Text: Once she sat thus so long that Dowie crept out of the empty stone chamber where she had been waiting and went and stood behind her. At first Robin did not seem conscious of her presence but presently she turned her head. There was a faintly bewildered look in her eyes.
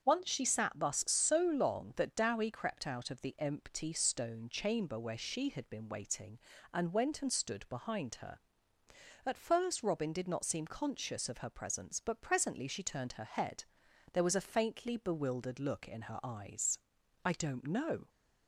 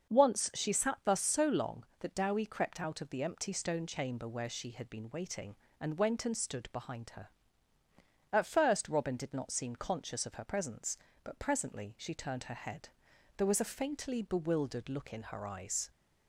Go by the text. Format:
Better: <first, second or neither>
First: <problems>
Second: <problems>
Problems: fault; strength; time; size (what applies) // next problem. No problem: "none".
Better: second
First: starts louder than the rest; until 1.0 s; 7 dB // goes on to say "I don't know"; noticeable; from 17.2 s on; 0.86 s long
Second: starts louder than the rest; until 1.2 s; 6.5 dB